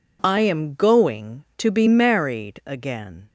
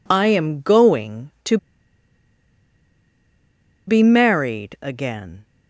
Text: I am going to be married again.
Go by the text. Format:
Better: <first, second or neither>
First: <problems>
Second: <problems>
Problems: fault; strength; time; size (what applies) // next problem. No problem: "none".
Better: first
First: none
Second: pauses between "to" and "be"; strong; at 1.5 s; 2.3 s long